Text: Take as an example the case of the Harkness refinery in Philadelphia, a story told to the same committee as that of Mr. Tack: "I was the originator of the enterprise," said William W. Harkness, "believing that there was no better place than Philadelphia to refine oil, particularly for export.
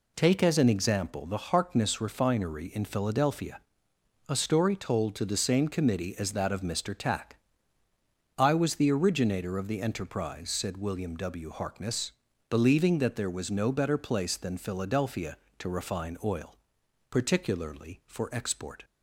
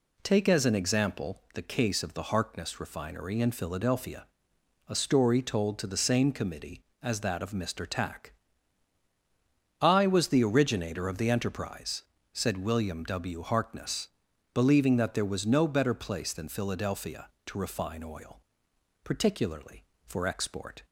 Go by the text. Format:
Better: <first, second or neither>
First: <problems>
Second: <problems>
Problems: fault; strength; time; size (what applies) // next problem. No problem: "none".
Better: second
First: skips "case of the"; at 1.5 s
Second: none